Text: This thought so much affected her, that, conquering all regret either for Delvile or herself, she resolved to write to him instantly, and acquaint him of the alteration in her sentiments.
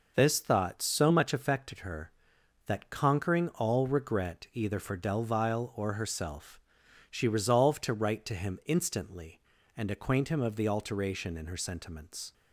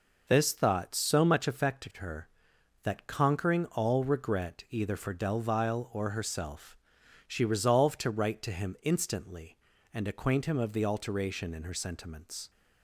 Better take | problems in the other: neither | none

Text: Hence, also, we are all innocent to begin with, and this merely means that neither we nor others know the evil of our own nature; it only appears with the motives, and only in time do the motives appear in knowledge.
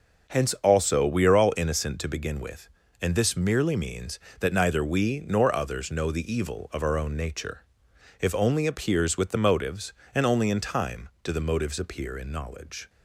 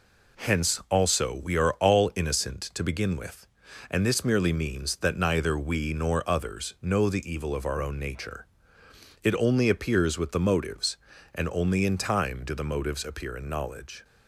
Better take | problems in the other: second | says "if" for "it"; at 8.1 s

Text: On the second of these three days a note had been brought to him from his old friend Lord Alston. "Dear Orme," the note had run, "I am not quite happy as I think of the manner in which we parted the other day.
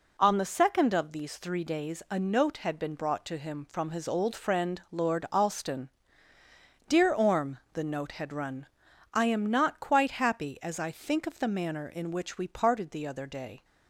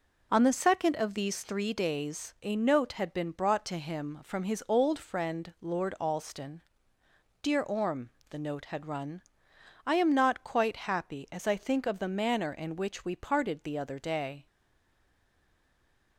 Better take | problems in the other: first | stays silent after the last word; noticeable; from 14.4 s on; 1.7 s long

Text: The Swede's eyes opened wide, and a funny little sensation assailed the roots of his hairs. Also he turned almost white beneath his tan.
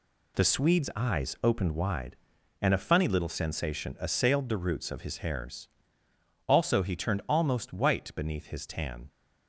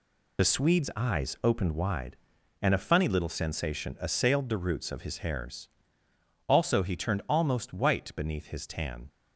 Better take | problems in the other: first | loses the start of "The"; at 0.3 s; 45 ms

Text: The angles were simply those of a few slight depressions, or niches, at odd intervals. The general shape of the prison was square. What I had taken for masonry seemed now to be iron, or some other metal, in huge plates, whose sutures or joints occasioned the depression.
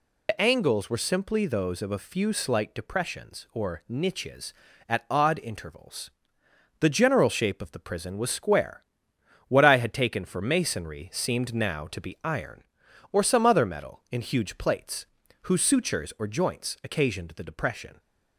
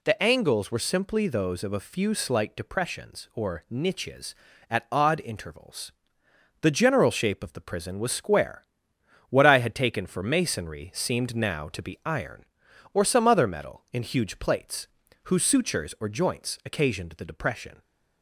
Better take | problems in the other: second | loses the start of "The"; at 0.2 s; 75 ms

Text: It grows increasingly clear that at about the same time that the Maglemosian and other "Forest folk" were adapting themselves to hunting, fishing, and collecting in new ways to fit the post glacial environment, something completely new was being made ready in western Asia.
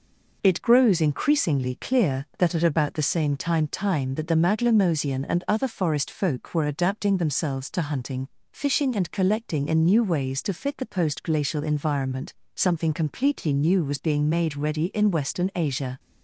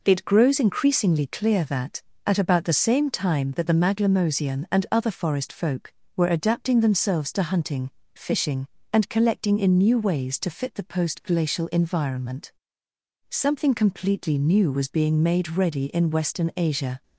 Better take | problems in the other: second | says "time" twice; at 3.6 s

